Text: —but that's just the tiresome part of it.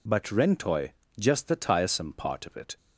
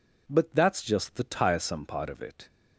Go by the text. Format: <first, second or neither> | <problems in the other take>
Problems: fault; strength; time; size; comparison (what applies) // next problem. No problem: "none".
second | says "rentoy" for "that's"; at 0.3 s